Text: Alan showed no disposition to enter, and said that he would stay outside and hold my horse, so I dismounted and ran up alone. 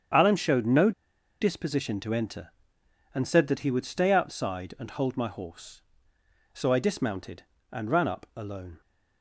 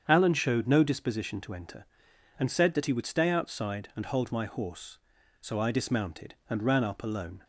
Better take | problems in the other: second | starts louder than the rest; strong; until 1.6 s; 8 dB; strong in the second // pauses between "no" and "disposition"; noticeable; at 0.9 s; 0.50 s long

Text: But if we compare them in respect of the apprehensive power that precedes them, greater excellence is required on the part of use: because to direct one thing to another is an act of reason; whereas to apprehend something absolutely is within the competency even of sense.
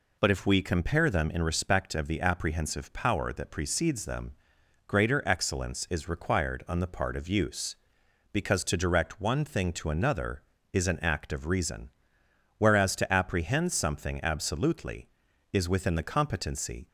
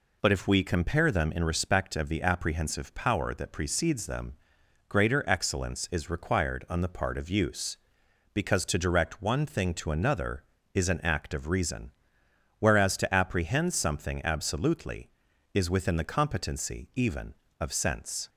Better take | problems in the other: second | stops before "even of sense"; at 16.8 s

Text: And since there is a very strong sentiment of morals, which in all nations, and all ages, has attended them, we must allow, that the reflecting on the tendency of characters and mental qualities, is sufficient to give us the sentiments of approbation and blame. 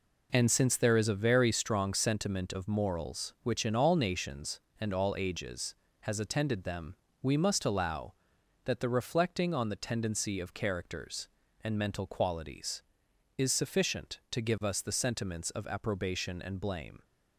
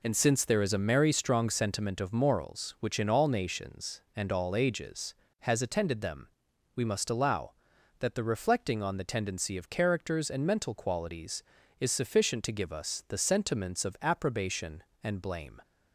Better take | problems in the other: first | says "merry" for "very"; at 0.7 s

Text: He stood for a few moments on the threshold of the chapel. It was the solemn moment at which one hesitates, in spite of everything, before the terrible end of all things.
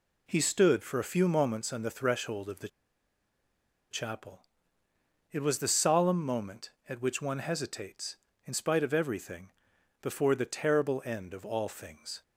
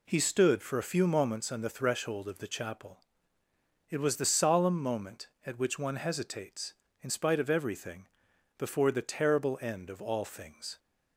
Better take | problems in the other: second | pauses between "the" and "chapel"; at 2.6 s; 1.2 s long

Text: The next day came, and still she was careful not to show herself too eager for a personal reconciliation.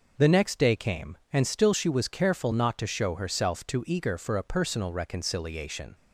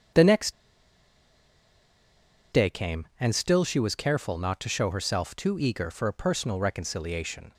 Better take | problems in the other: first | starts louder than the rest; strong; until 3.2 s; 8 dB // pauses between "next" and "day"; strong; at 0.5 s; 1.9 s long

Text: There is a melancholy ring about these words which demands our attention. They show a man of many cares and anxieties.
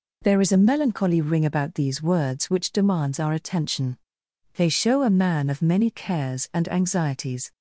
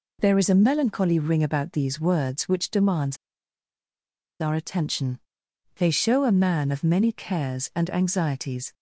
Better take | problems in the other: first | pauses between "demands" and "our"; at 3.1 s; 1.2 s long

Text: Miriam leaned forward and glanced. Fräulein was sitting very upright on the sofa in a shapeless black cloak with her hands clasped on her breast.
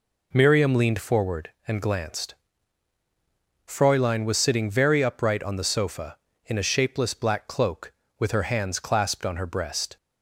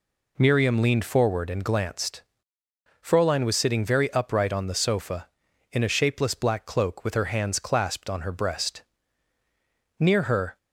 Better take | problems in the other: first | goes on to say "Near her"; from 9.9 s on; 0.58 s long

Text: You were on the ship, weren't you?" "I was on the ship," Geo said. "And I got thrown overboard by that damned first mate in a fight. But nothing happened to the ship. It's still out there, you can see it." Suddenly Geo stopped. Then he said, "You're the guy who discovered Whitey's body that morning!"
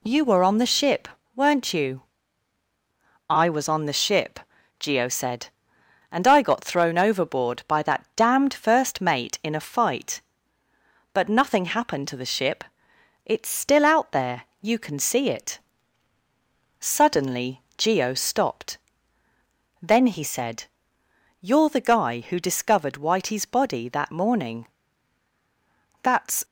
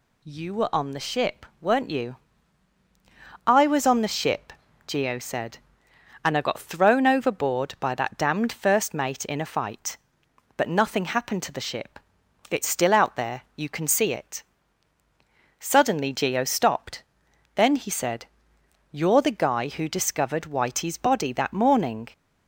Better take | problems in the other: second | pauses between "Suddenly" and "Geo"; slight; at 17.6 s; 0.16 s long // goes on to say "That's"; slight; from 26.0 s on; 0.42 s long

